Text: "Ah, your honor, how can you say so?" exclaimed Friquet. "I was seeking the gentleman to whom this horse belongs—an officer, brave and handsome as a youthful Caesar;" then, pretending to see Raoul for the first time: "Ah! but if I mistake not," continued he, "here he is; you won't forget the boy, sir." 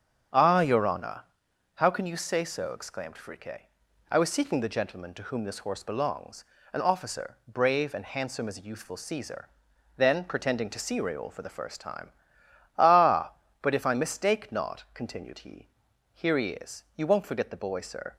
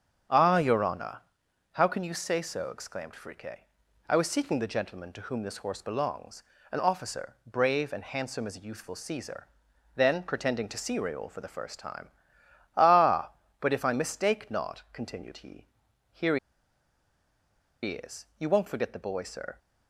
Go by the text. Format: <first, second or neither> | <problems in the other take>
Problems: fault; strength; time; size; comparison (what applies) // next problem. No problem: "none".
first | starts louder than the rest; strong; until 1.8 s; 8 dB; strong in the first // pauses between "here" and "he"; strong; at 16.3 s; 1.4 s long